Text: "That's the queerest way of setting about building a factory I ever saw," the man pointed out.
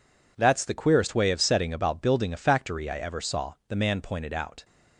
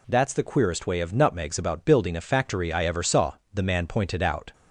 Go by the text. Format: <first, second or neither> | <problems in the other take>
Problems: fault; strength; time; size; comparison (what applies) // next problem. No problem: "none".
first | says "nutmegs" for "setting"; at 1.1 s